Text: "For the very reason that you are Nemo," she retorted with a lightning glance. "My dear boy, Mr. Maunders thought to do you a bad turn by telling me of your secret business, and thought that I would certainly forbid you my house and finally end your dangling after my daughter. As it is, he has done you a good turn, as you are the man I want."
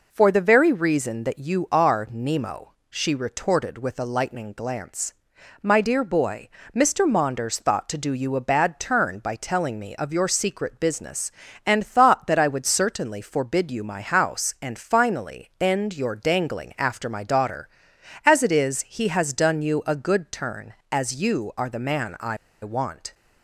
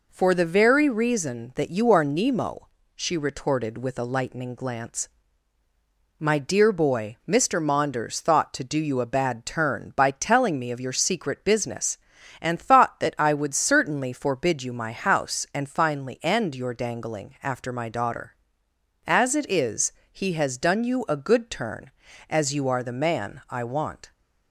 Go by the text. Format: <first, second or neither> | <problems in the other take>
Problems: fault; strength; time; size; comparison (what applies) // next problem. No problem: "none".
second | pauses between "I" and "want"; slight; at 22.3 s; 0.25 s long